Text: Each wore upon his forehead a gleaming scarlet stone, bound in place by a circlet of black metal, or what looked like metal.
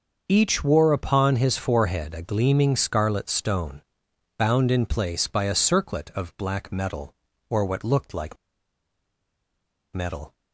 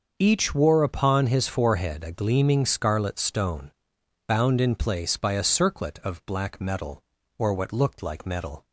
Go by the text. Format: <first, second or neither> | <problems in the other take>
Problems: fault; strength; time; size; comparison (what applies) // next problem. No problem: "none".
second | starts louder than the rest; until 1.2 s; 6 dB; also in the second // pauses between "like" and "metal"; strong; at 8.3 s; 1.5 s long